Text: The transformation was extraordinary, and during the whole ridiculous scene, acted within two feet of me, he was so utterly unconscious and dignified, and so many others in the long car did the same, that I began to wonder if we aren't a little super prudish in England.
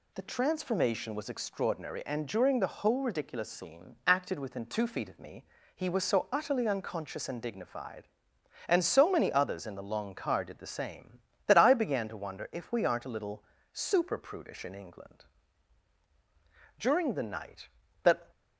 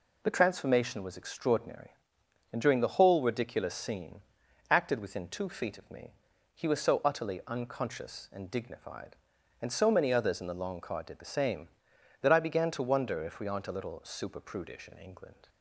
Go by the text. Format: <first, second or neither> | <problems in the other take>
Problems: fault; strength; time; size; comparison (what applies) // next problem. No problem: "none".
second | pauses between "little" and "super"; slight; at 13.4 s; 0.28 s long // goes on to say "During the night that"; from 16.7 s on; 1.5 s long